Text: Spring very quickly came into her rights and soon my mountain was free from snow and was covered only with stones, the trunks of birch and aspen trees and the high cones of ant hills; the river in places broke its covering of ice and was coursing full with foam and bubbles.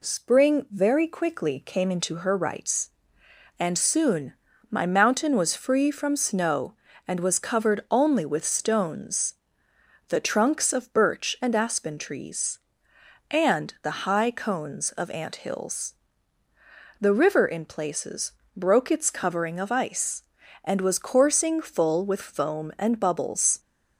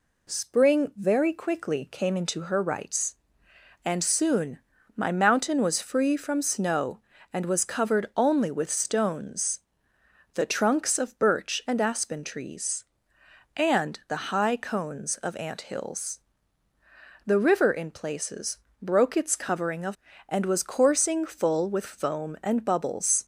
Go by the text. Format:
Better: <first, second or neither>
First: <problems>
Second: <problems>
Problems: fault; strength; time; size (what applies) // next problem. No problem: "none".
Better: first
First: pauses between "soon" and "my"; slight; at 4.3 s; 0.36 s long // pauses between "places" and "broke"; slight; at 18.3 s; 0.24 s long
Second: pauses between "soon" and "my"; slight; at 4.5 s; 0.36 s long // pauses between "places" and "broke"; slight; at 18.5 s; 0.24 s long // skips "ice"; at 20.1 s